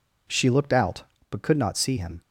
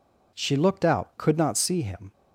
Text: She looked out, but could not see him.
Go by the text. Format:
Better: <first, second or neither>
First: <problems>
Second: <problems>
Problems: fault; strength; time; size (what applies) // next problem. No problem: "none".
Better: first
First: none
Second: skips "but"; at 1.1 s